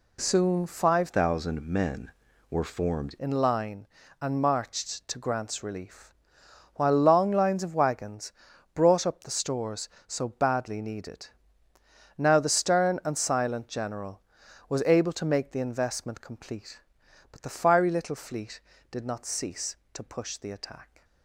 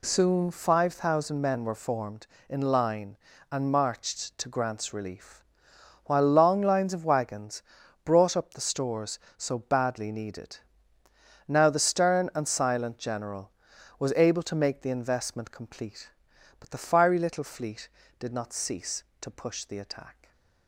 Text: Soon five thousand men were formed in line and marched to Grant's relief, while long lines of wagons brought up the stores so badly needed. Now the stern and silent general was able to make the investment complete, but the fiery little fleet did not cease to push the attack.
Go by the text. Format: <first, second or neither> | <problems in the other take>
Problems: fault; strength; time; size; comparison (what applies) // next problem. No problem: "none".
second | changes voice from "thousand" to "formed"; from 1.0 to 3.1 s; 2.1 s long // pauses between "wagons" and "brought"; at 8.3 s; 0.42 s long; also in the second